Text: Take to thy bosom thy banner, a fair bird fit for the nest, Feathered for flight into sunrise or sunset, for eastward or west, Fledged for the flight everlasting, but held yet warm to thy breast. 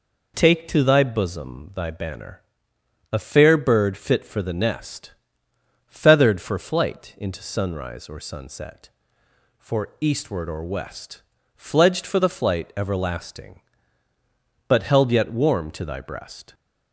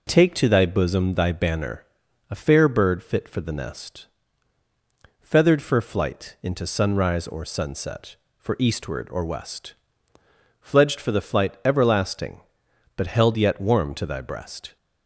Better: neither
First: none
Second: none

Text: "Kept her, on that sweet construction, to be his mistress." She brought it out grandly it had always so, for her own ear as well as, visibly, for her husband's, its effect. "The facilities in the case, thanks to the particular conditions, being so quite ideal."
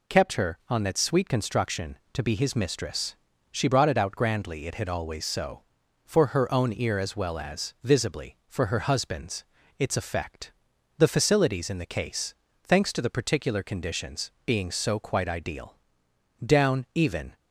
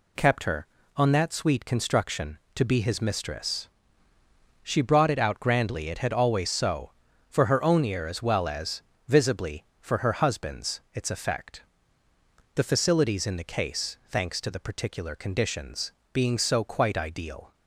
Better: second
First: goes on to say "Down even"; noticeable; from 16.4 s on; 0.90 s long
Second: none

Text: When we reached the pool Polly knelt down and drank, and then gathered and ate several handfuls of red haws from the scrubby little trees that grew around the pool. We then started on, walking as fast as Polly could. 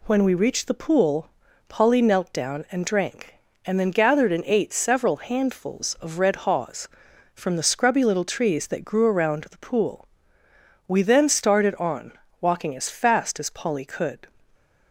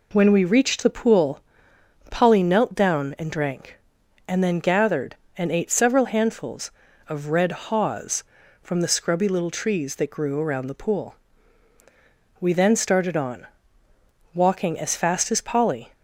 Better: first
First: pauses between "pool" and "Polly"; at 1.2 s; 0.38 s long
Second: pauses between "pool" and "Polly"; noticeable; at 1.3 s; 0.70 s long // stops before "could"; at 15.9 s

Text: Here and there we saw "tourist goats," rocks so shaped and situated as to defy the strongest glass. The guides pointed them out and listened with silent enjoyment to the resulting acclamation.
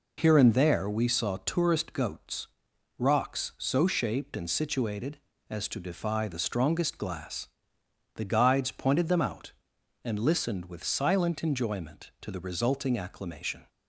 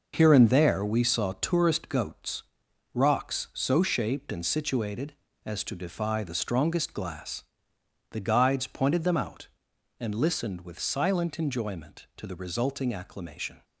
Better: first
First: none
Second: gets quieter; strong; throughout; 8.5 dB

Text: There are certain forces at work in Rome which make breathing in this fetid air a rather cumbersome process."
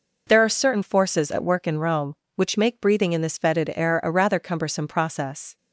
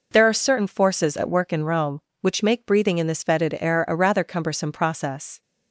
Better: neither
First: none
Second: none

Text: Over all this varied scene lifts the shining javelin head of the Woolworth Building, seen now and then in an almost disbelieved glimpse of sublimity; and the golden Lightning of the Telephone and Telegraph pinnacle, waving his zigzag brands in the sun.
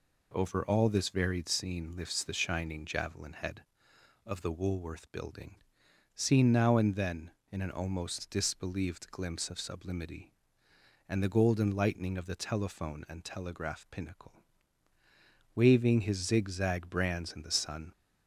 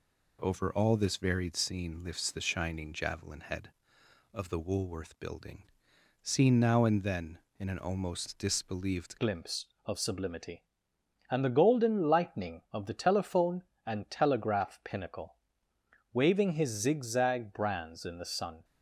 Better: first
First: none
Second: changes voice at "glimpse"; from 9.1 s on; 9.5 s long

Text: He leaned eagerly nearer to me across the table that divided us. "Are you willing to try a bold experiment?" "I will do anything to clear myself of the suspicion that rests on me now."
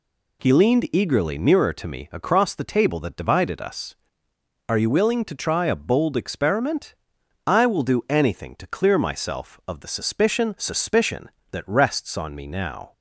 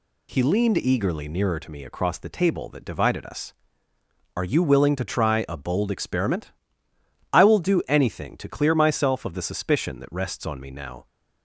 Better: second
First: says "suspicion" twice; at 10.5 s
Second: none

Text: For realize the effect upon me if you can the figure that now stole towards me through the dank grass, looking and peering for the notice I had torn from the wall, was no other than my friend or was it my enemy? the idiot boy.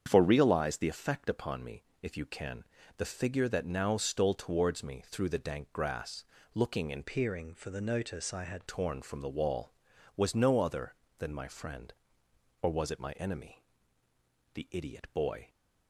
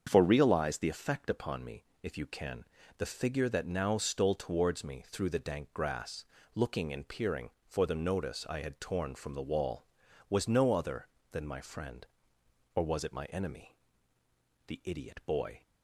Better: second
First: starts louder than the rest; strong; until 1.0 s; 7.5 dB // pauses between "me" and "if"; slight; at 1.8 s; 0.18 s long // pauses between "can" and "the"; slight; at 2.6 s; 0.34 s long // changes voice from "peering" to "had"; from 7.0 to 8.6 s; 1.6 s long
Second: starts louder than the rest; strong; until 1.0 s; 7 dB // pauses between "me" and "if"; slight; at 1.8 s; 0.18 s long // pauses between "can" and "the"; slight; at 2.6 s; 0.34 s long

